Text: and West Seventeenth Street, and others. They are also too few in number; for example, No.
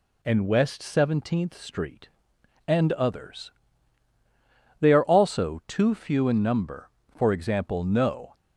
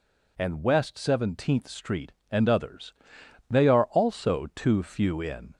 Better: first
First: none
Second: stops before "number for example No"; at 5.5 s

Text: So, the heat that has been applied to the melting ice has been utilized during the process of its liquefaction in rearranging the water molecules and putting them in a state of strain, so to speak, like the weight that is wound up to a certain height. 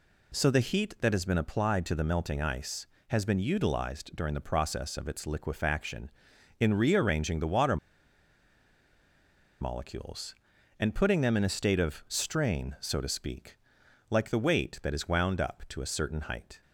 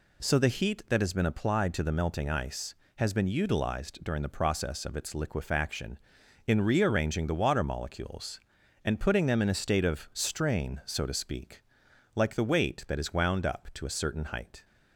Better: second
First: pauses between "water" and "molecules"; strong; at 7.7 s; 1.8 s long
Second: none

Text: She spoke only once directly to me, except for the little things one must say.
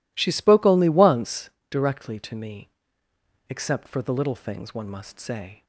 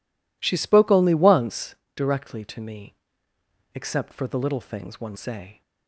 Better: first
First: pauses between "once" and "directly"; slight; at 1.4 s; 0.22 s long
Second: pauses between "once" and "directly"; slight; at 1.7 s; 0.22 s long // skips "must"; at 5.1 s

